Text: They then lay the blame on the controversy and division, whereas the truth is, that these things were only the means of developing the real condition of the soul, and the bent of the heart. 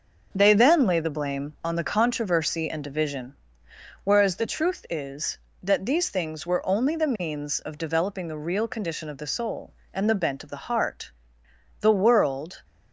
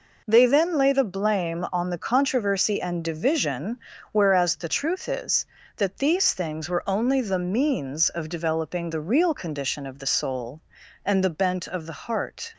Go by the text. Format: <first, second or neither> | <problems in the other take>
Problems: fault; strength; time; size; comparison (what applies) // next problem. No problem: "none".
second | starts louder than the rest; noticeable; until 1.3 s; 6 dB // goes on to say "The world"; noticeable; from 11.8 s on; 0.82 s long